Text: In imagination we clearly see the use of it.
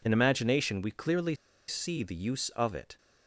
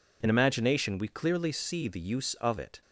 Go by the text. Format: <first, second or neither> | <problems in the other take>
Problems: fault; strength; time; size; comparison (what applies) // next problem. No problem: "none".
second | pauses between "clearly" and "see"; slight; at 1.3 s; 0.34 s long